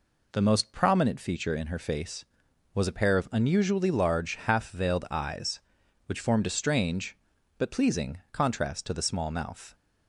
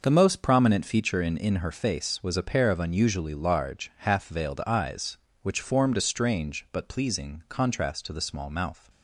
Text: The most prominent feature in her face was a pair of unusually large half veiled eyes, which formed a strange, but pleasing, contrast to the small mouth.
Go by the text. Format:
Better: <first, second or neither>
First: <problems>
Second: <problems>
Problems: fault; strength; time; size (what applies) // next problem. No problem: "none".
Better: first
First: none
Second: says "in" twice; at 1.3 s